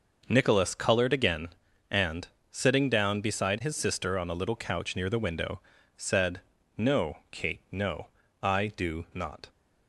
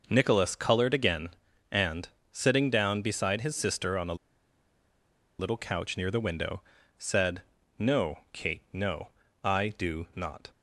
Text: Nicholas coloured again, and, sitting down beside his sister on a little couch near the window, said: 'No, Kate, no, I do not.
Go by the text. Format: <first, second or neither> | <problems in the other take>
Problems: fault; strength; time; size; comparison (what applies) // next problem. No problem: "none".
first | pauses between "a" and "little"; at 4.1 s; 1.2 s long